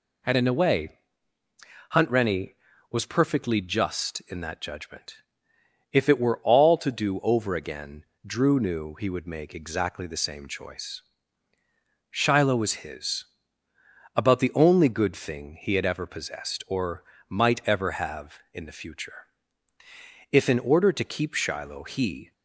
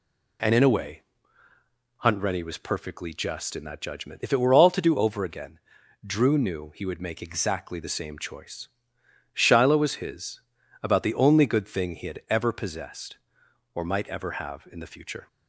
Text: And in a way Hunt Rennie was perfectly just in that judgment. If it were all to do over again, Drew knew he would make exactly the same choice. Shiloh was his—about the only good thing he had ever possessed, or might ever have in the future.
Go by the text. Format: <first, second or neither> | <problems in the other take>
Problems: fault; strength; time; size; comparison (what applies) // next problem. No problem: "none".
second | pauses between "way" and "Hunt"; at 0.9 s; 1.0 s long; noticeable in the second // pauses between "or" and "might"; slight; at 17.0 s; 0.26 s long // goes on to say "If in order to keep Shiloh he"; strong; from 20.3 s on; 2.0 s long